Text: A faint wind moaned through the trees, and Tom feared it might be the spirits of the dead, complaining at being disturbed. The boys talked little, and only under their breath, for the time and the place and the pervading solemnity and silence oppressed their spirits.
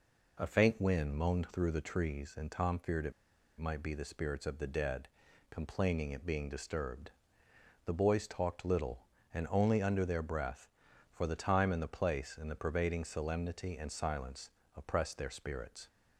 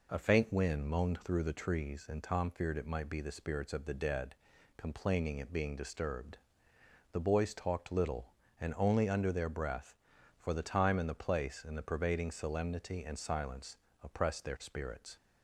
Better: second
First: pauses between "it" and "might"; noticeable; at 3.1 s; 0.46 s long // pauses between "silence" and "oppressed"; slight; at 14.4 s; 0.26 s long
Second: pauses between "silence" and "oppressed"; slight; at 13.7 s; 0.26 s long

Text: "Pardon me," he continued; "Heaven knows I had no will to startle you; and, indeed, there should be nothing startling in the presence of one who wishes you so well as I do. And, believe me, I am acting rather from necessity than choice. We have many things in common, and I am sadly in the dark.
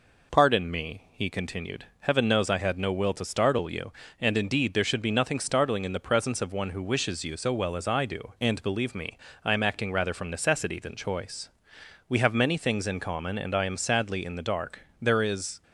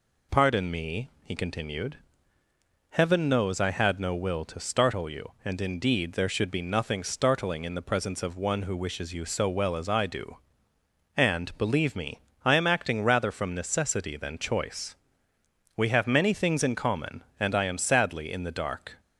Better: second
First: goes on to say "There is"; from 15.0 s on; 0.60 s long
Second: none

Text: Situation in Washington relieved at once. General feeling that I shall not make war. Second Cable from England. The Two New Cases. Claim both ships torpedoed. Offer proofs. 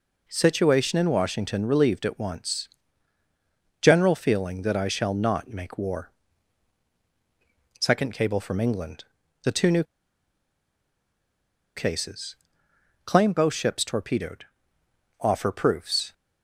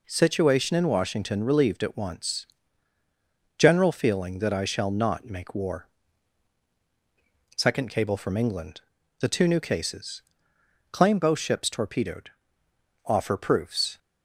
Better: second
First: pauses between "New" and "Cases"; strong; at 9.8 s; 1.9 s long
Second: none

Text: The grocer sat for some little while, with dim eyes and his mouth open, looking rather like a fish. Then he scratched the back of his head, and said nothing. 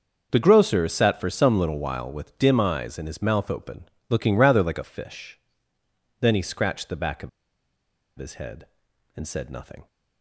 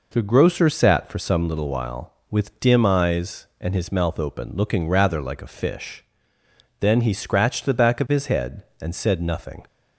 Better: second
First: starts louder than the rest; until 1.3 s; 6 dB // pauses between "of" and "his"; noticeable; at 7.2 s; 0.88 s long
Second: none

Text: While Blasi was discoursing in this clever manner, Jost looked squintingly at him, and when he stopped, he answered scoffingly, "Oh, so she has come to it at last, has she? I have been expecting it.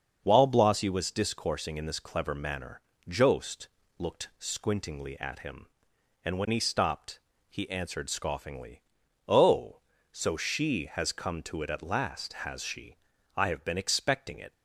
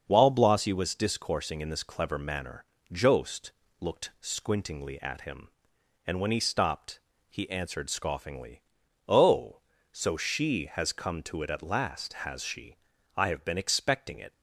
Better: neither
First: starts louder than the rest; until 1.2 s; 6.5 dB // pauses between "Jost" and "looked"; slight; at 3.6 s; 0.30 s long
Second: starts louder than the rest; until 1.0 s; 6.5 dB // pauses between "Jost" and "looked"; slight; at 3.5 s; 0.28 s long

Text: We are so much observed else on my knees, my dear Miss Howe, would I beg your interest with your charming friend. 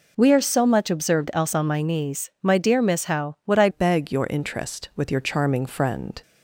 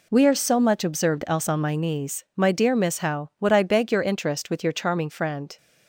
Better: second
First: changes voice at "beg"; from 3.6 s on; 2.6 s long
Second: none

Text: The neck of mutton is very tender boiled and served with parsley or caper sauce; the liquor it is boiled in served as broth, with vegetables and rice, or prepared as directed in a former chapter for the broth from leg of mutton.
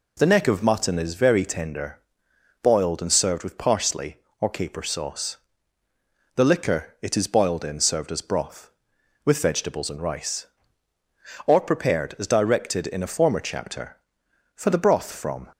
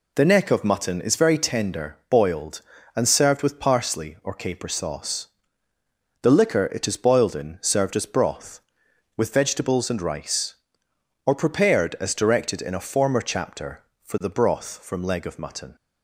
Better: second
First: pauses between "tender" and "boiled"; noticeable; at 1.9 s; 0.64 s long // stops before "leg of mutton"; at 15.5 s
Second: none

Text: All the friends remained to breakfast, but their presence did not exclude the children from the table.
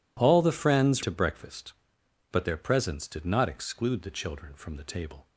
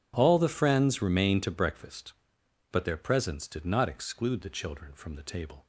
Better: second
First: skips "remained"; at 1.0 s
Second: none

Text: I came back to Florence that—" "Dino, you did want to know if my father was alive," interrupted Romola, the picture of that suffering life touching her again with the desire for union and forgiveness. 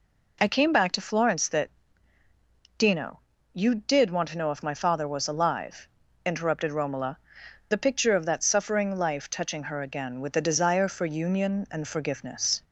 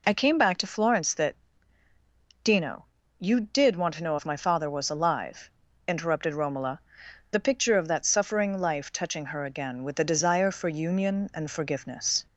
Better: neither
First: none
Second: none

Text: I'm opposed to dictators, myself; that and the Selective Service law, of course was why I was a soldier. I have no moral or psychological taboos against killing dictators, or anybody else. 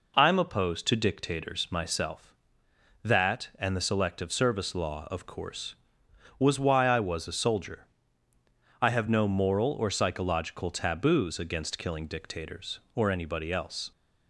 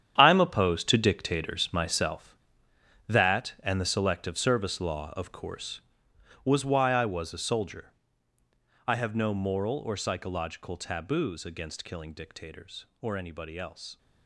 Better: first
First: none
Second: gets quieter; strong; throughout; 12.5 dB

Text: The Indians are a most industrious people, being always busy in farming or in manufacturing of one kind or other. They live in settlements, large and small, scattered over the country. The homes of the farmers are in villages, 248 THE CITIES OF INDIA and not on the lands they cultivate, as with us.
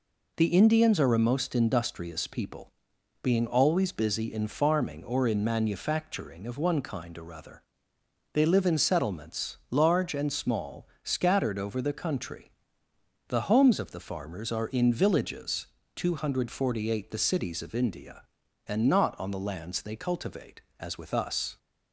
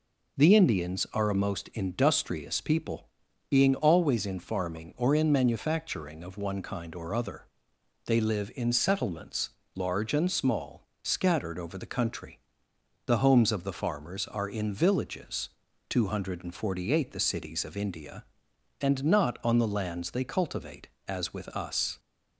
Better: first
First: none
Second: skips "busy"; at 4.2 s

